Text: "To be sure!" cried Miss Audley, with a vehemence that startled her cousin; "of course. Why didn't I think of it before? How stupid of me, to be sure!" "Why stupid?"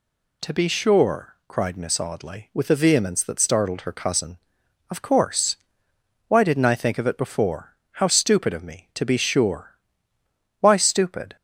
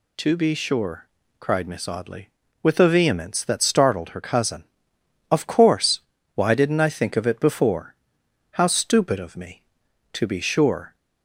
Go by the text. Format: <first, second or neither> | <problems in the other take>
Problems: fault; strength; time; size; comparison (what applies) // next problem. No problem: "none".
first | stops before "Why stupid"; at 10.9 s